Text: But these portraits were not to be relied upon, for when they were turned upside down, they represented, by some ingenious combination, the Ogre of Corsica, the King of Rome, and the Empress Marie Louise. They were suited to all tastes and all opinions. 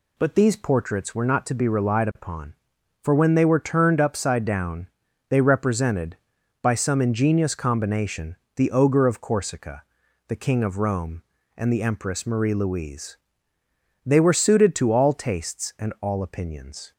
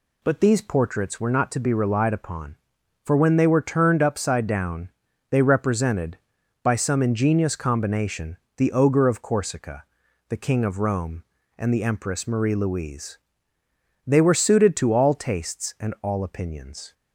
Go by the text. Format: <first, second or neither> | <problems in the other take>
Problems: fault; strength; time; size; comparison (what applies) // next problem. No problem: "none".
neither | none